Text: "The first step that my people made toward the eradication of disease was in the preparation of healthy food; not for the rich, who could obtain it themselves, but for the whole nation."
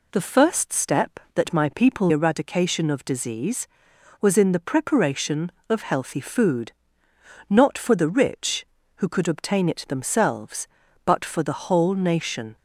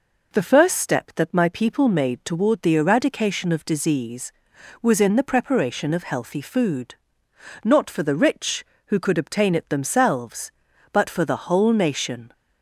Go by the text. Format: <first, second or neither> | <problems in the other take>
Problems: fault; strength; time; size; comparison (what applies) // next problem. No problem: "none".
second | skips "made toward the"; at 2.1 s